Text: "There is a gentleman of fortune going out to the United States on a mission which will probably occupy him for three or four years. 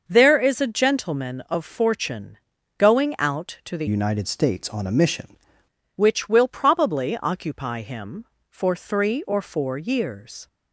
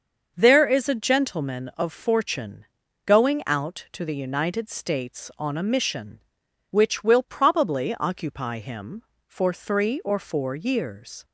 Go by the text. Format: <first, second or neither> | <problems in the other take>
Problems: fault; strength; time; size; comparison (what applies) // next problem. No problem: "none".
second | starts louder than the rest; until 1.0 s; 6 dB; also in the second // pauses between "fortune" and "going"; at 2.3 s; 0.40 s long; also in the second // changes voice from "United" to "mission"; from 3.8 to 5.2 s; 1.4 s long